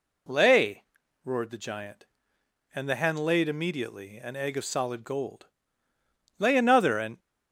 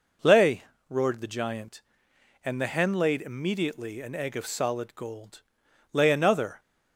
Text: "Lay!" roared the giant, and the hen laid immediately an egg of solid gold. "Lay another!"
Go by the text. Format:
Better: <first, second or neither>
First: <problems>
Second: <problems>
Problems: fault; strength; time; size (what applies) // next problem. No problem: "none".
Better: second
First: goes on to say "and"; slight; from 6.9 s on; 0.20 s long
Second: none